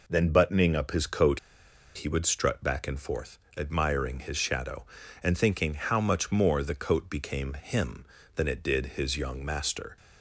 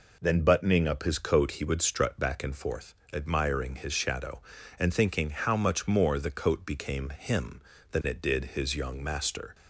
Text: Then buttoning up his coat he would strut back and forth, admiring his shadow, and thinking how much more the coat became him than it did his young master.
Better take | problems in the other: second | pauses between "coat" and "he"; noticeable; at 1.3 s; 0.57 s long

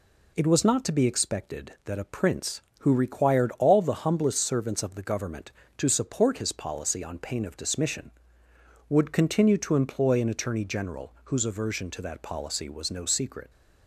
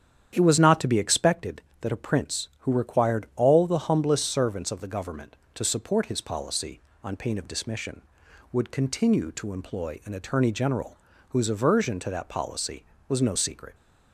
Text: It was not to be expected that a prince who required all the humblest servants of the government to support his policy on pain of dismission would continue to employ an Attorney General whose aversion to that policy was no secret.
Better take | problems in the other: first | starts louder than the rest; strong; until 1.4 s; 9 dB // pauses between "General" and "whose"; slight; at 10.9 s; 0.32 s long

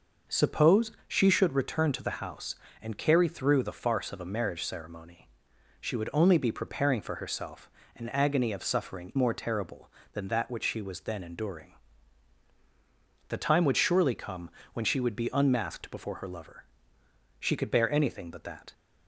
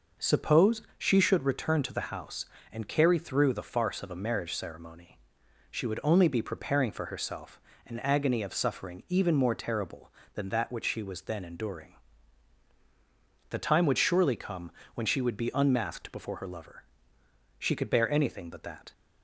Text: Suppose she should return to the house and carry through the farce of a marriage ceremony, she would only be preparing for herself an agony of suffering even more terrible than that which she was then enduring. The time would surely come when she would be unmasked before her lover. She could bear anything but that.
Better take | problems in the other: second | pauses between "Suppose" and "she"; slight; at 0.9 s; 0.16 s long; slight in the second // pauses between "herself" and "an"; slight; at 7.6 s; 0.26 s long; slight in the second // skips "even"; at 9.1 s // pauses between "come" and "when"; slight; at 14.5 s; 0.22 s long; slight in the second

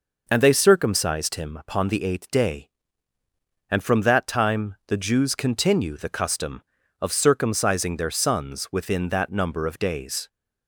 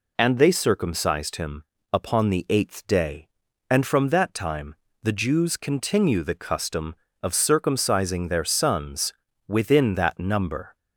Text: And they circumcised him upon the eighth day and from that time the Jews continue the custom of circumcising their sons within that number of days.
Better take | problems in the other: first | pauses between "him" and "upon"; slight; at 1.6 s; 0.28 s long // pauses between "time" and "the"; slight; at 4.7 s; 0.28 s long // pauses between "sons" and "within"; slight; at 9.1 s; 0.34 s long // stops before "of days"; at 10.7 s

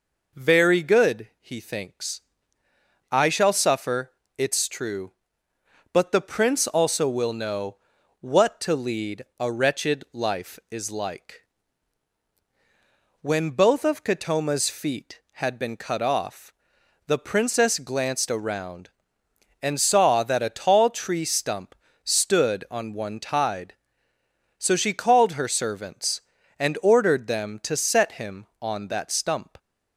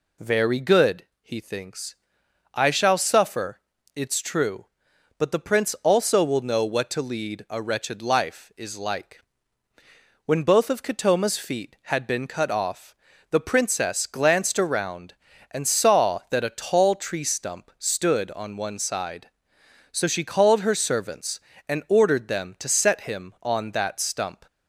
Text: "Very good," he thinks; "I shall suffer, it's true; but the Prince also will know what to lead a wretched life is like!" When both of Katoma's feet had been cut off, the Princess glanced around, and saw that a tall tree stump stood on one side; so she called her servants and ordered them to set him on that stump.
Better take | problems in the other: second | pauses between "know" and "what"; at 7.7 s; 0.42 s long // pauses between "stump" and "stood"; slight; at 21.7 s; 0.26 s long // says "tide" for "side"; at 23.1 s

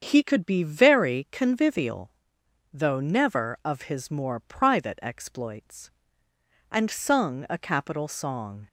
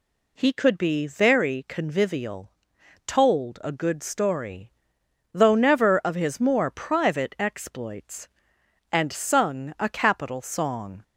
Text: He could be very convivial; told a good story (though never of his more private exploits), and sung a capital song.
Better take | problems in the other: second | starts louder than the rest; strong; until 1.0 s; 7 dB // skips "told a good story"; at 2.4 s

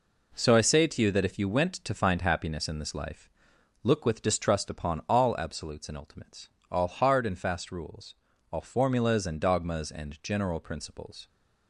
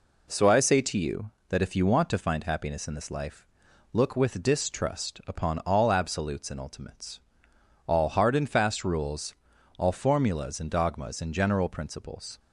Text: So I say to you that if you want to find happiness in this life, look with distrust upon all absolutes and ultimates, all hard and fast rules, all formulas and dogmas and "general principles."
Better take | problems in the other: second | says "went" for "want"; at 1.4 s

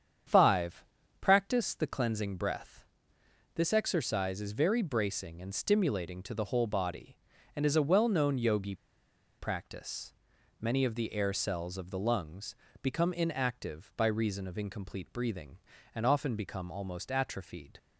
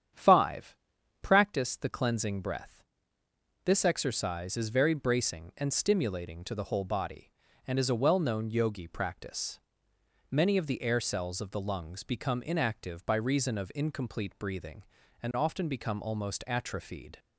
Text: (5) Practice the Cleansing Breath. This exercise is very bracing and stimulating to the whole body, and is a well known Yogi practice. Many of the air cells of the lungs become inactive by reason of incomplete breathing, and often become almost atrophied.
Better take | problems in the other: second | starts louder than the rest; strong; until 1.6 s; 8 dB; strong in the second // pauses between "Yogi" and "practice"; noticeable; at 8.7 s; 0.64 s long // pauses between "lungs" and "become"; slight; at 12.5 s; 0.26 s long

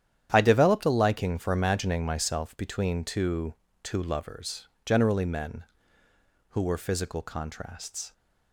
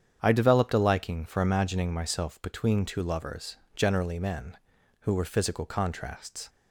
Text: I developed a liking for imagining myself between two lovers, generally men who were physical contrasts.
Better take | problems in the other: second | starts louder than the rest; strong; until 1.3 s; 10 dB; strong in the second // says "two" twice; at 3.8 s

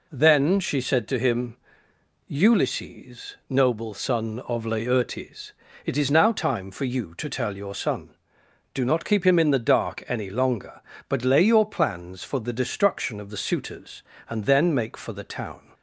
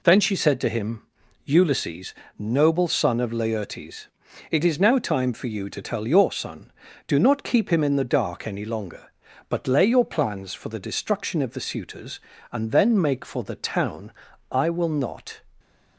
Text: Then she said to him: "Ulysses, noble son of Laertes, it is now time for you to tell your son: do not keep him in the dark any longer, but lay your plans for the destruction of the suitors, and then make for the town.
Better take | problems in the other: first | goes on to say "I will not"; noticeable; from 14.5 s on; 0.88 s long

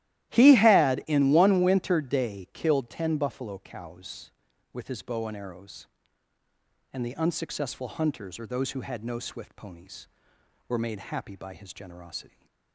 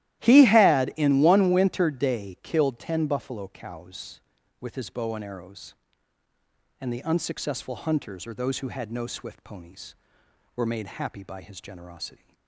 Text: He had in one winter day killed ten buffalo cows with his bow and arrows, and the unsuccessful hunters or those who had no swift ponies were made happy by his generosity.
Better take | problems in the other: neither | starts louder than the rest; strong; the same in both

